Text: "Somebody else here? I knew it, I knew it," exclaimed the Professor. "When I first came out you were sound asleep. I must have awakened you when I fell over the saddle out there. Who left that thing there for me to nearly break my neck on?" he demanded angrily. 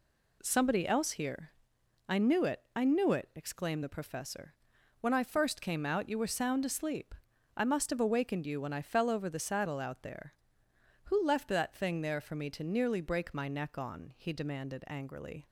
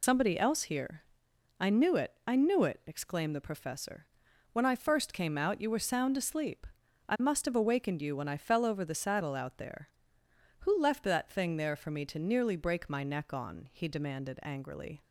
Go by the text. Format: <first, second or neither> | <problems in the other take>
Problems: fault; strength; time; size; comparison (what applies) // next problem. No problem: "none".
first | loses the start of "Somebody"; at 0.0 s; 110 ms